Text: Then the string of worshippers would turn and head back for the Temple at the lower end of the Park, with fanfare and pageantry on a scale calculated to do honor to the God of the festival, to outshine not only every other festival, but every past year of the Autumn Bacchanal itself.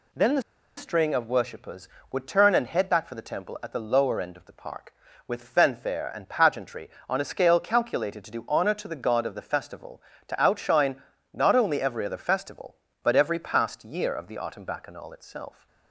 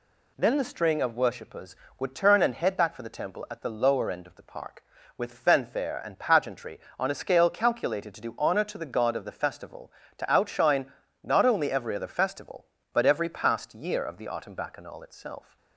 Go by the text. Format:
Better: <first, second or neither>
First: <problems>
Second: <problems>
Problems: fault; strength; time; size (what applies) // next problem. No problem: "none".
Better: second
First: pauses between "the" and "string"; slight; at 0.4 s; 0.35 s long // pauses between "outshine" and "not"; slight; at 11.0 s; 0.30 s long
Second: pauses between "outshine" and "not"; slight; at 10.9 s; 0.30 s long